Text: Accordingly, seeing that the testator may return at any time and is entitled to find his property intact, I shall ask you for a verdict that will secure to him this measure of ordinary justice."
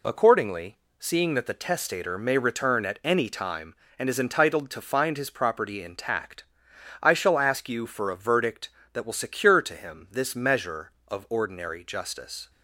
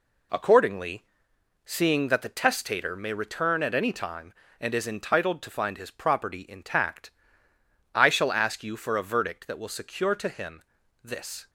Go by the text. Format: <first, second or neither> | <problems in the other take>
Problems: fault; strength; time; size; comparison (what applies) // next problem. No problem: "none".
first | pauses between "him" and "this"; at 10.6 s; 0.42 s long // stops before "measure of ordinary justice"; at 11.4 s